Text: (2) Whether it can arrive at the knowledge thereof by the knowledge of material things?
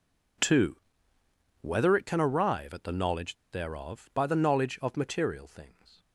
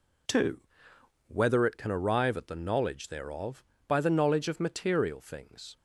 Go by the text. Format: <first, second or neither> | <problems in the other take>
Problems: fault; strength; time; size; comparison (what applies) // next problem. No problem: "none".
second | pauses between "knowledge" and "thereof"; slight; at 3.3 s; 0.18 s long